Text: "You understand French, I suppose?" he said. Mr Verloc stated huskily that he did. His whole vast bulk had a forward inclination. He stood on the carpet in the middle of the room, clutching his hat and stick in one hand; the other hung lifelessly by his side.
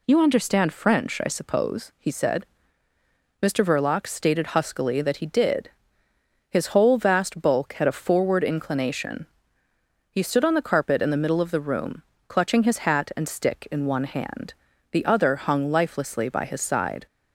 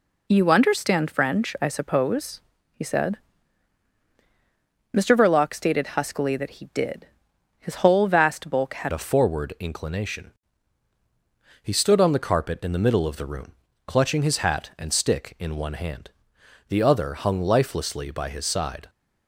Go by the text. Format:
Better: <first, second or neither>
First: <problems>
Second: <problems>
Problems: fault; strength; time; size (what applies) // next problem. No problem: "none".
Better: first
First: none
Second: changes voice at "a"; from 8.9 s on; 9.9 s long